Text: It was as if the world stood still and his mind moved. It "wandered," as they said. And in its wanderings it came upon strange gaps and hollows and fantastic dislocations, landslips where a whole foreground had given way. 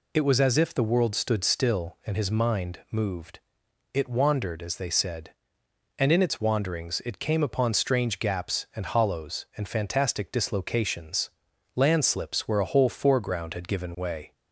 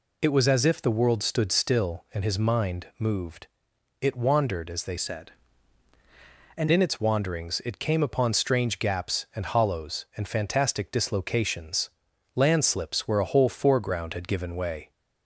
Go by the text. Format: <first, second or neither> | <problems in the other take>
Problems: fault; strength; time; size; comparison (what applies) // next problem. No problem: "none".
first | changes voice from "said" to "And"; from 4.9 to 6.6 s; 1.7 s long